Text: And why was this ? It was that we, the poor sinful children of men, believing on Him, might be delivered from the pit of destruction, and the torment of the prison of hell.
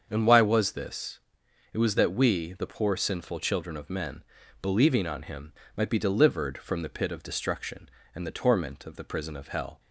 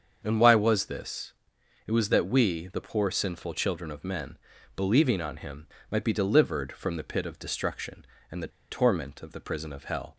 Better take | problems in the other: first | starts louder than the rest; until 1.2 s; 7 dB; also in the first // pauses between "the" and "torment"; slight; at 8.4 s; 0.23 s long

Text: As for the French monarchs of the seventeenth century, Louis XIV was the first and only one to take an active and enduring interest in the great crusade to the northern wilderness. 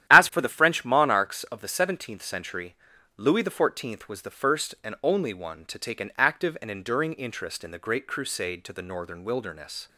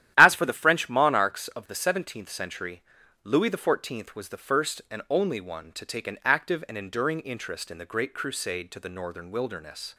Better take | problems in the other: neither | starts louder than the rest; strong; the same in both

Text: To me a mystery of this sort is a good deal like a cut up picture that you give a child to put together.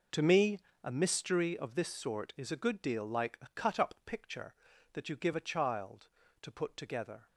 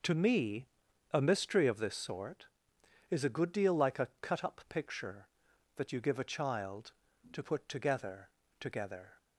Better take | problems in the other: first | pauses between "me" and "a"; at 0.6 s; 0.44 s long; slight in the first // says "together" twice; at 8.5 s

